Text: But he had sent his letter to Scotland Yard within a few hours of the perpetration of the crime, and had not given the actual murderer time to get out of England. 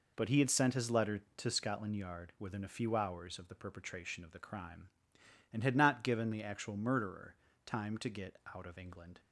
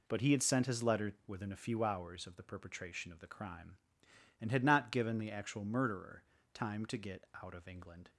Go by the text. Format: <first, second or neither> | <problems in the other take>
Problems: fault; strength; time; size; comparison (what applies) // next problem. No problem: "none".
first | skips "to Scotland Yard"; at 1.1 s // pauses between "murderer" and "time"; slight; at 6.2 s; 0.32 s long; slight in the first // pauses between "get" and "out"; slight; at 7.2 s; 0.18 s long; slight in the first